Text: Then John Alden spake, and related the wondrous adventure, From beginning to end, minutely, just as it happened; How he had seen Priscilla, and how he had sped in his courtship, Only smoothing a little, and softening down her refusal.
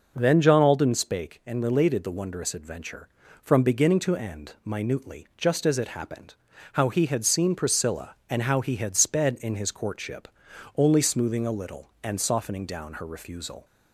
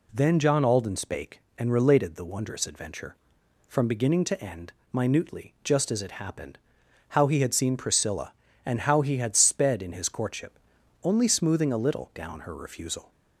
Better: first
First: none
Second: skips "and softening"; at 12.1 s

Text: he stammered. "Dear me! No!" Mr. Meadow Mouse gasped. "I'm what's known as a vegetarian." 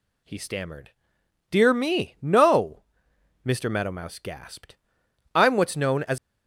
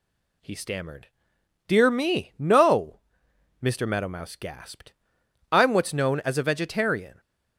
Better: second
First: stops before "a vegetarian"; at 6.1 s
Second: none

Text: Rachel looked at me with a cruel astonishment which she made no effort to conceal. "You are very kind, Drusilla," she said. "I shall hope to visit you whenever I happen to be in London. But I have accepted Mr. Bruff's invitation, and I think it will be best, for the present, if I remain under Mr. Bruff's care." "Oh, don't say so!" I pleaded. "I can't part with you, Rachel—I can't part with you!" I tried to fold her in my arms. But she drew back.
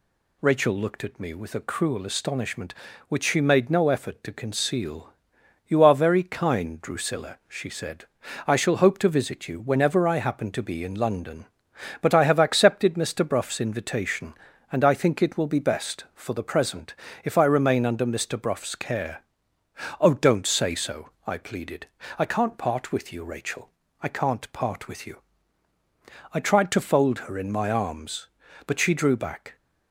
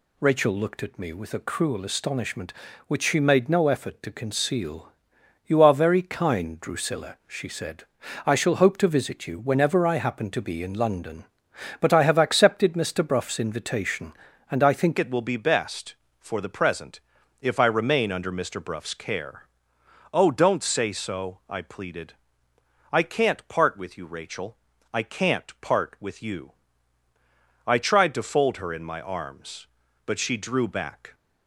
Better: first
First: none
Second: changes voice at "it"; from 14.9 s on; 16.2 s long

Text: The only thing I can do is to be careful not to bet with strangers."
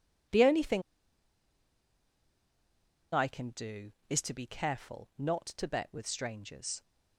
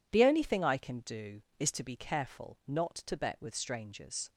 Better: second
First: pauses between "thing" and "I"; strong; at 0.8 s; 2.3 s long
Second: none

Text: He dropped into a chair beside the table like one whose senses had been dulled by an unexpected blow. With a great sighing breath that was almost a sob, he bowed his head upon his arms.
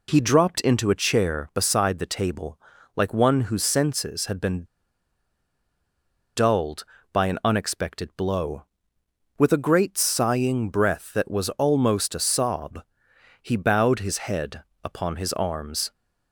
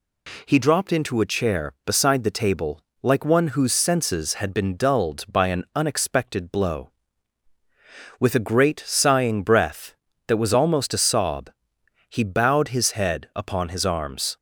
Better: second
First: pauses between "table" and "like"; at 2.5 s; 0.38 s long // pauses between "been" and "dulled"; strong; at 4.6 s; 1.7 s long // pauses between "head" and "upon"; slight; at 14.6 s; 0.18 s long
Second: pauses between "table" and "like"; slight; at 2.8 s; 0.22 s long

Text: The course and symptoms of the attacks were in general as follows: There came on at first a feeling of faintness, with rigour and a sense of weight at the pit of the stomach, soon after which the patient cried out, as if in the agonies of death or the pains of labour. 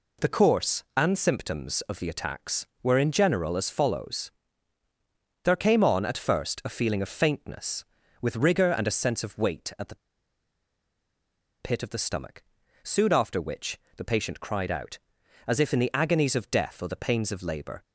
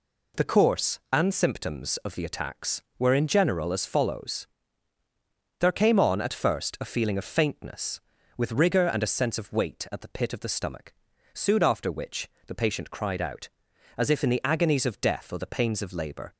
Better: second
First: pauses between "the" and "pit"; strong; at 9.9 s; 1.6 s long // pauses between "which" and "the"; slight; at 13.7 s; 0.16 s long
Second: pauses between "which" and "the"; slight; at 12.3 s; 0.16 s long

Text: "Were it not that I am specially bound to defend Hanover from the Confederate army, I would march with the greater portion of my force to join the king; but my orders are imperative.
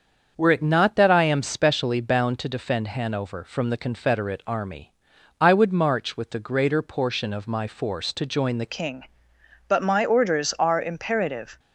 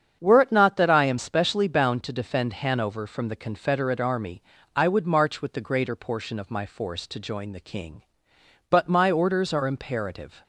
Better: second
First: starts louder than the rest; until 1.3 s; 7 dB // changes voice at "king"; from 8.7 s on; 2.8 s long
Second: starts louder than the rest; strong; until 1.2 s; 8 dB

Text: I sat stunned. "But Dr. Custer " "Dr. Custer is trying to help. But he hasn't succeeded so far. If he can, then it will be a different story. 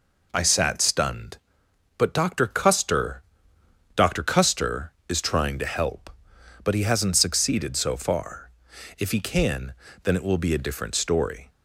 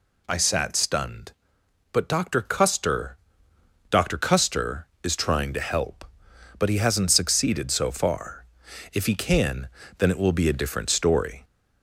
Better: first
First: none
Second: gets louder; noticeable; throughout; 5.5 dB

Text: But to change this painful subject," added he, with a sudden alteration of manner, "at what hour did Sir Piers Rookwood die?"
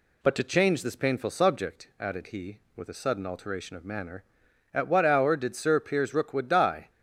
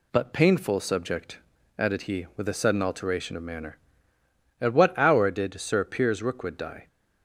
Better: first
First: none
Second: skips "to change this"; at 0.3 s

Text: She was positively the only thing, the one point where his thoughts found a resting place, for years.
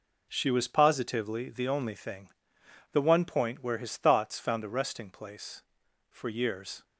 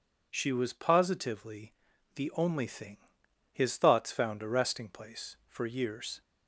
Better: first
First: none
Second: pauses between "positively" and "the"; at 1.7 s; 0.42 s long // skips "the one point where"; at 3.2 s

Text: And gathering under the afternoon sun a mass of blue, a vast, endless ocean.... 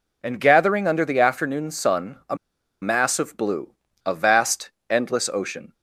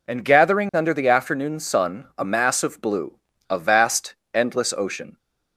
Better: second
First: pauses between "a" and "mass"; noticeable; at 2.3 s; 0.46 s long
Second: none

